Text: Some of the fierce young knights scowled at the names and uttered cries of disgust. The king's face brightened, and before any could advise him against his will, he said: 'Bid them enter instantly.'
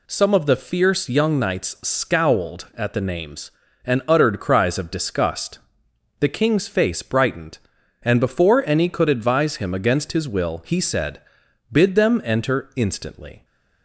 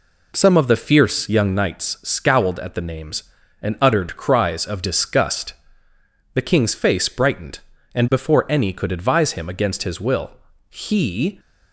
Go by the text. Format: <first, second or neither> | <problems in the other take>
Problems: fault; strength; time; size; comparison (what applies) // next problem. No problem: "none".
first | stops before "said Bid them enter instantly"; at 11.3 s